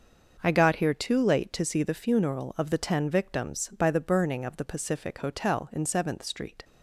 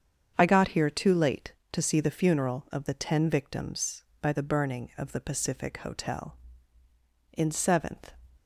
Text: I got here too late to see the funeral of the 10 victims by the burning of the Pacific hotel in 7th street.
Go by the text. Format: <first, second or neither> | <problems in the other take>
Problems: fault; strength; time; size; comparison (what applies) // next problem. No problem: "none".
first | starts louder than the rest; strong; until 1.3 s; 7.5 dB; also in the first // stops before "street"; at 8.3 s